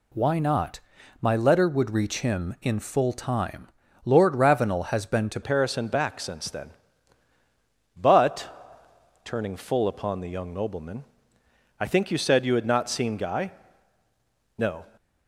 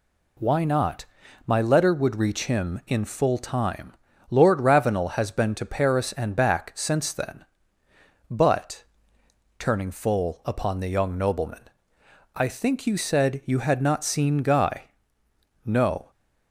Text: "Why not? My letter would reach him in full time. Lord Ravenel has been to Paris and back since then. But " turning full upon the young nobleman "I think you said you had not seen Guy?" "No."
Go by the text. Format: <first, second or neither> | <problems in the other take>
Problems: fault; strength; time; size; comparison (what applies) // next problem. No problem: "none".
second | changes voice at "Paris"; from 5.4 s on; 9.4 s long // pauses between "nobleman" and "I"; noticeable; at 11.0 s; 0.76 s long; noticeable in the second